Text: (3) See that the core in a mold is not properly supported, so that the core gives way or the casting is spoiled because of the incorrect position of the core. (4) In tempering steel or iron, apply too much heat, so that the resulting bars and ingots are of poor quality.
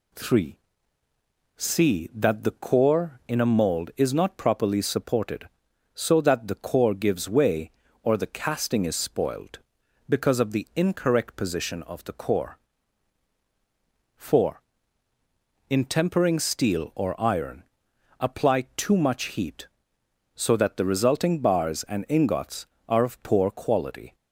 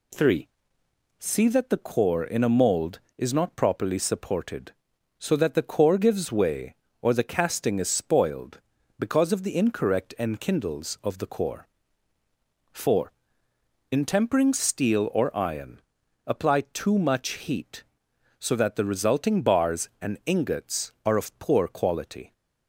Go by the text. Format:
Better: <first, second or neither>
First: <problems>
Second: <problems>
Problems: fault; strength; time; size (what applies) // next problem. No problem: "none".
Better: first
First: none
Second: says "enkindles" for "position"; at 10.1 s